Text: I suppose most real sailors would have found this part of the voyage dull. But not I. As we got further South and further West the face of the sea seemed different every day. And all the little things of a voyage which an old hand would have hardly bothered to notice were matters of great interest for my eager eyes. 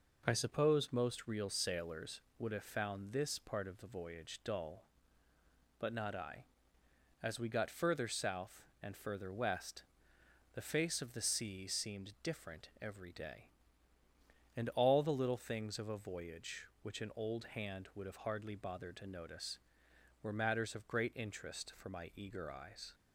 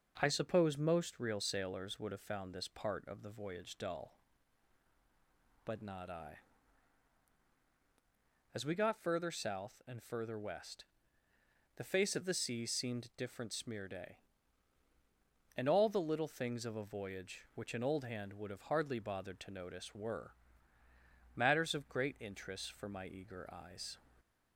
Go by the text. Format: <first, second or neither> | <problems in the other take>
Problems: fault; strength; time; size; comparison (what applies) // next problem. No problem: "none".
first | pauses between "West" and "the"; noticeable; at 10.8 s; 0.92 s long; noticeable in the first // says "smear" for "every"; at 13.5 s // pauses between "were" and "matters"; at 20.3 s; 1.0 s long